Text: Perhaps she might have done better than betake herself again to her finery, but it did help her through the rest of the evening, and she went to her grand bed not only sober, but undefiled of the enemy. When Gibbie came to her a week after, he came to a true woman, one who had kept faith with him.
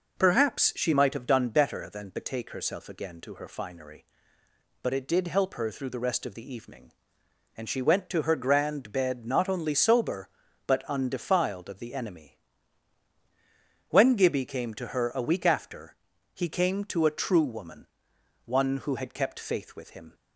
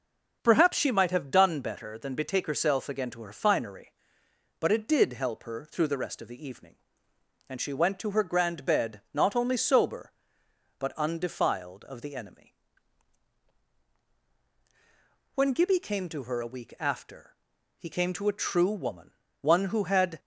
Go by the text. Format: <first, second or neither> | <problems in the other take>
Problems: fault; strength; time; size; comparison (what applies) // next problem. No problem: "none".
first | stops before "kept faith with him"; at 20.1 s